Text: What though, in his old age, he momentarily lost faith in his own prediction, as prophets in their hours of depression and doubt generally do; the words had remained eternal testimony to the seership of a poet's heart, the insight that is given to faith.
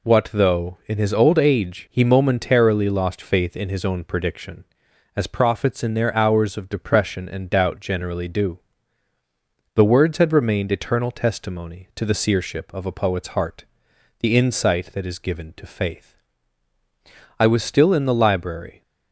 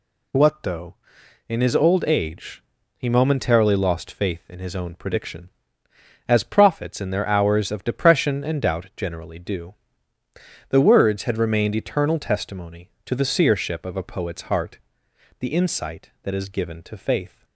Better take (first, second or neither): second